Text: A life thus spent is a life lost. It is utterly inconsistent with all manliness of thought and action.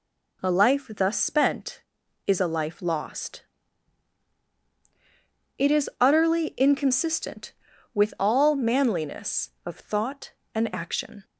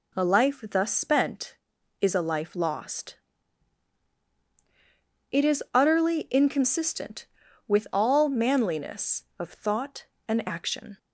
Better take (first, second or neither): neither